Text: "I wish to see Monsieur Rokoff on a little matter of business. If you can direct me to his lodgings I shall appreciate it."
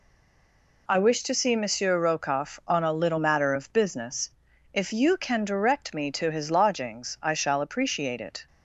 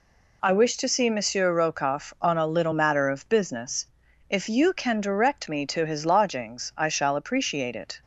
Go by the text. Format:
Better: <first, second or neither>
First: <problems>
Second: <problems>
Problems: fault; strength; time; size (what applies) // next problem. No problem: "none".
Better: second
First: stays silent before the first word; slight; until 0.8 s; 0.8 s long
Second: none